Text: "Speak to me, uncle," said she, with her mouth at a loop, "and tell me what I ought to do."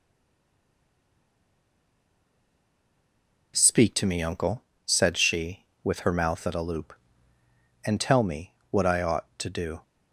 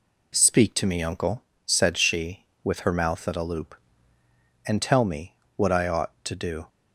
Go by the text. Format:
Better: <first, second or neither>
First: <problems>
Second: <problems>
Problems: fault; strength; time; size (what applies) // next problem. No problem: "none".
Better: second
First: stays silent before the first word; strong; until 3.5 s; 3.5 s long // pauses between "me" and "what"; slight; at 8.5 s; 0.16 s long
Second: pauses between "me" and "what"; slight; at 5.3 s; 0.21 s long